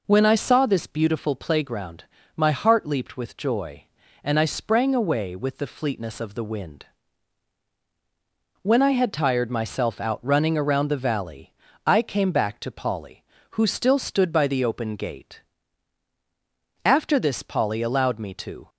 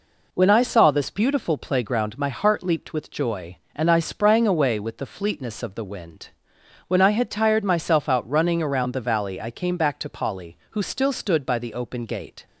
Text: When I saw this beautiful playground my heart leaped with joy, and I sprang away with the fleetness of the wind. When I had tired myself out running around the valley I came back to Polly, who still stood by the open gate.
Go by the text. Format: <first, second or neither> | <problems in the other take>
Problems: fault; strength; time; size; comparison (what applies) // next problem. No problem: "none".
second | pauses between "playground" and "my"; slight; at 2.0 s; 0.34 s long // pauses between "valley" and "I"; slight; at 11.5 s; 0.34 s long // goes on to say "After this Polly allowed me to"; strong; from 16.8 s on; 1.8 s long